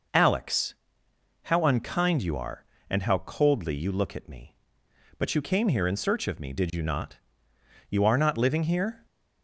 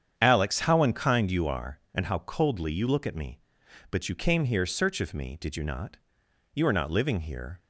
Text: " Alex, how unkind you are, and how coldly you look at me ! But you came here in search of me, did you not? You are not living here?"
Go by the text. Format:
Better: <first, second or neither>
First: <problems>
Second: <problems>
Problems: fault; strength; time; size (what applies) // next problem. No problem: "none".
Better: first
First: none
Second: starts louder than the rest; strong; until 1.1 s; 8 dB // skips "in"; at 4.6 s